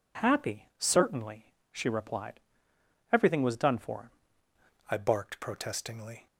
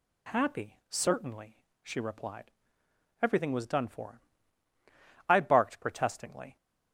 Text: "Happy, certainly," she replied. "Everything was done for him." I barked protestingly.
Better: second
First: changes voice at "I"; from 4.8 s on; 1.4 s long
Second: none

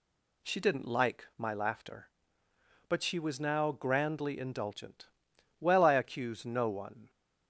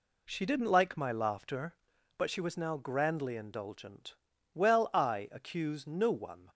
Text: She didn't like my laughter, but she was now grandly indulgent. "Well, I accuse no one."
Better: neither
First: none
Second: none

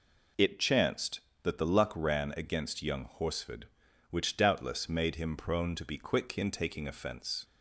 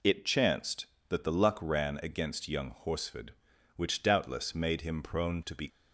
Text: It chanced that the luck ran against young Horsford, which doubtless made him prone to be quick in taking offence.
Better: first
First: none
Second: stops before "quick in taking offence"; at 5.6 s

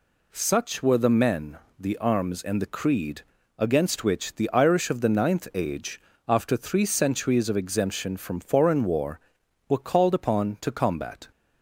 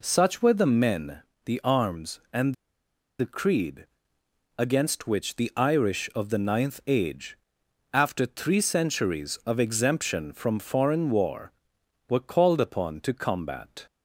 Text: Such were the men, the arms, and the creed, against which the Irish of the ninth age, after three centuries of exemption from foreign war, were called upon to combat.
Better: first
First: none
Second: pauses between "and" and "the"; noticeable; at 2.5 s; 0.65 s long

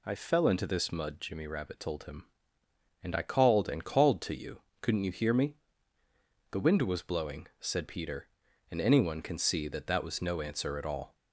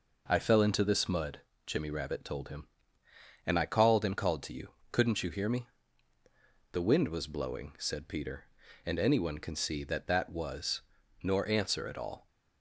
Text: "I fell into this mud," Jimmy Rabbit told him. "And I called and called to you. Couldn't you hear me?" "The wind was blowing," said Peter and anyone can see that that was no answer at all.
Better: first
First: none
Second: says "nor" for "no"; at 11.2 s

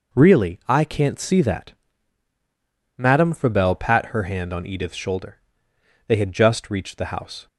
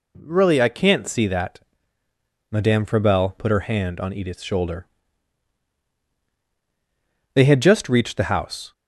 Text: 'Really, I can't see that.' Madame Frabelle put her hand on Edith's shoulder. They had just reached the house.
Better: second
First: says "pat" for "put"; at 3.7 s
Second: none

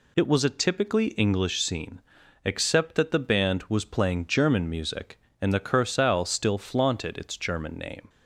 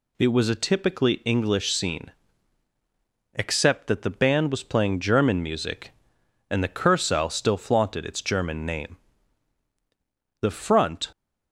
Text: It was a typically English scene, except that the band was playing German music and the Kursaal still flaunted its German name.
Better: first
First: none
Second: goes on to say "The front"; noticeable; from 10.4 s on; 0.70 s long

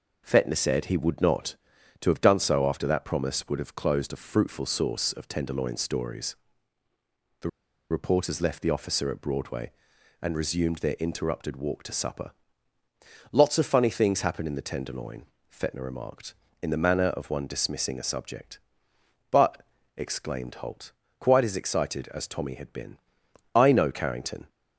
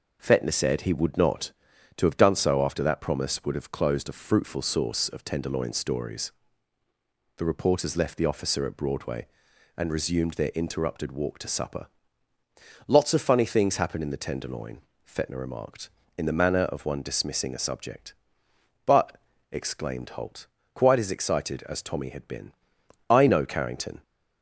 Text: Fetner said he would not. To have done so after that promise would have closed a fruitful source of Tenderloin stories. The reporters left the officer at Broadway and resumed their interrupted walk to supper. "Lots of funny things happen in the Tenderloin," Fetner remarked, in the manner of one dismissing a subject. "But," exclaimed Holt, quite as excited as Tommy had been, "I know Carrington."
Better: second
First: pauses between "The" and "reporters"; at 7.4 s; 0.43 s long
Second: none

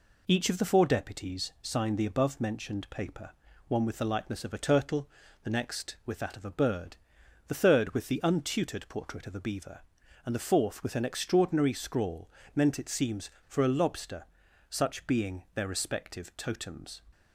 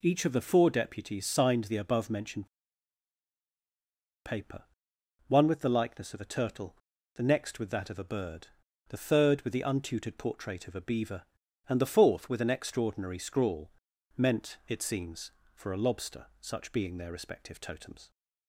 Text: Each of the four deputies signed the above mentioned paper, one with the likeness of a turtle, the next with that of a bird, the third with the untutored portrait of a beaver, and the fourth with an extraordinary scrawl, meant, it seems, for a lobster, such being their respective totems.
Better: first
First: none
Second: pauses between "mentioned" and "paper"; strong; at 2.4 s; 1.7 s long

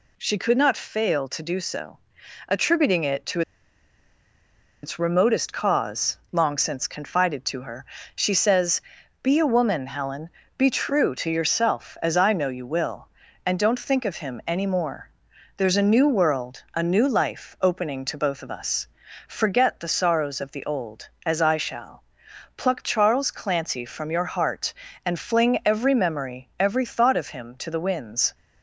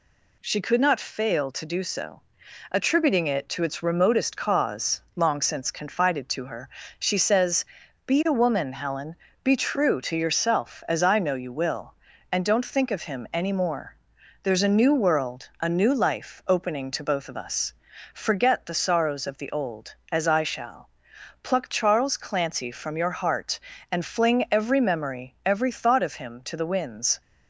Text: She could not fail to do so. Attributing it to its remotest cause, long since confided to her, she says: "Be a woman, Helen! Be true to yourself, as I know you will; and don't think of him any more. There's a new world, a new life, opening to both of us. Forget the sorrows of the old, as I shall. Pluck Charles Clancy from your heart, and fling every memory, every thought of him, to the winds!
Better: second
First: pauses between "to" and "its"; strong; at 3.4 s; 1.4 s long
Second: none

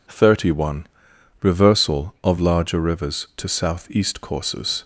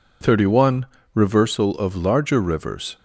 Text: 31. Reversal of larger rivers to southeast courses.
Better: first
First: none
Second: stops before "to southeast courses"; at 2.9 s

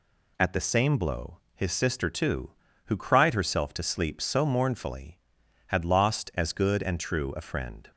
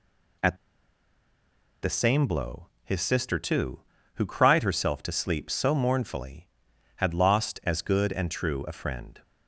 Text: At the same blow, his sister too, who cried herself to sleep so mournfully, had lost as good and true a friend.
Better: first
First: none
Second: pauses between "At" and "the"; strong; at 0.5 s; 1.2 s long

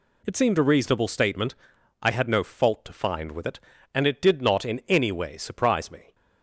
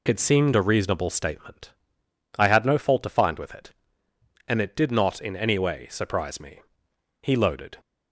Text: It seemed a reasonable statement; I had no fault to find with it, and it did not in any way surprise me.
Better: first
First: none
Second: goes on to say "He loaded"; from 7.2 s on; 0.58 s long

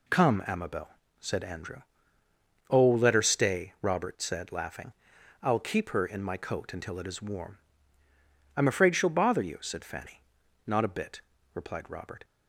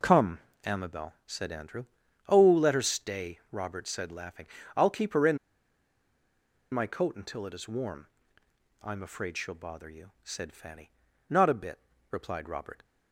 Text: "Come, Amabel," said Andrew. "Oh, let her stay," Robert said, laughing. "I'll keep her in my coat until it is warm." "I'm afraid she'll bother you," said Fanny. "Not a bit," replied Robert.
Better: first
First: none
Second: pauses between "in" and "my"; strong; at 5.3 s; 1.3 s long

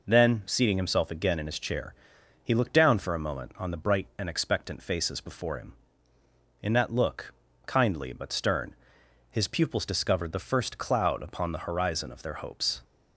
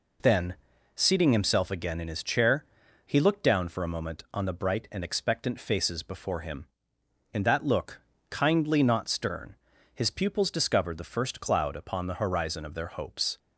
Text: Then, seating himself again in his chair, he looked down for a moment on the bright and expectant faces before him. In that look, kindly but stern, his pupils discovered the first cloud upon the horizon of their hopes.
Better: first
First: none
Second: says "not" for "but"; at 8.8 s

